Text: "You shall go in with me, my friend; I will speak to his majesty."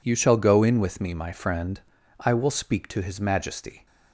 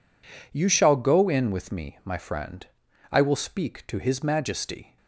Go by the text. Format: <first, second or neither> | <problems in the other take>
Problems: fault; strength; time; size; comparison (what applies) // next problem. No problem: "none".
neither | none